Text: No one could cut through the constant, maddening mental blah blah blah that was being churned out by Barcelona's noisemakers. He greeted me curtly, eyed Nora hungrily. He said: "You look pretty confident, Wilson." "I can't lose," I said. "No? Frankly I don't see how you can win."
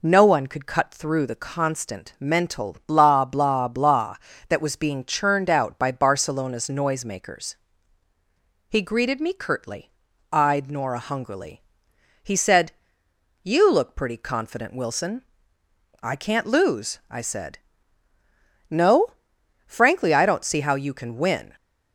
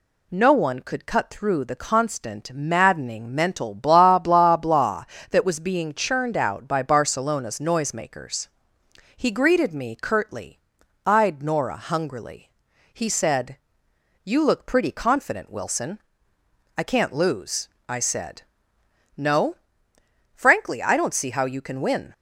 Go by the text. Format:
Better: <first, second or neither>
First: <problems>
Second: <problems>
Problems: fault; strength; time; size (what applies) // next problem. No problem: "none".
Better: second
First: skips "maddening"; at 2.1 s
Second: none